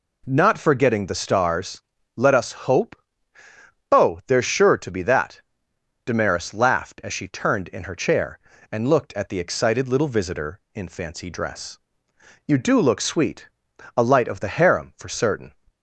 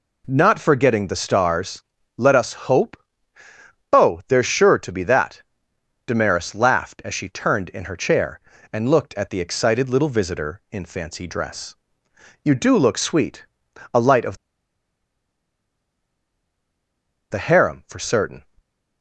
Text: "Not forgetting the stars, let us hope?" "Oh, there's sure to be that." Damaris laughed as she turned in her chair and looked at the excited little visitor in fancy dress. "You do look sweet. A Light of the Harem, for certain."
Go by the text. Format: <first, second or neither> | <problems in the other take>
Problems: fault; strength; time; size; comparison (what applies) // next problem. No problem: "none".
first | pauses between "of" and "the"; strong; at 14.3 s; 2.9 s long